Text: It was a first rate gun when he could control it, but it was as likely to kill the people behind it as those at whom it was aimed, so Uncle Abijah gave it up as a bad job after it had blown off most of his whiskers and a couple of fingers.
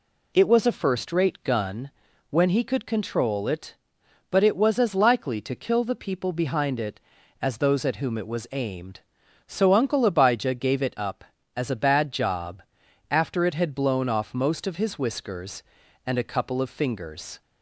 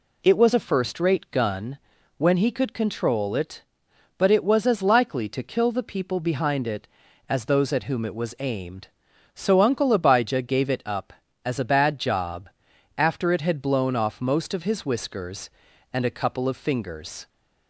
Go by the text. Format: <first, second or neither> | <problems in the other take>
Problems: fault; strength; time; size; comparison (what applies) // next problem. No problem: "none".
neither | pauses between "gun" and "when"; the same in both // pauses between "job" and "after"; noticeable; the same in both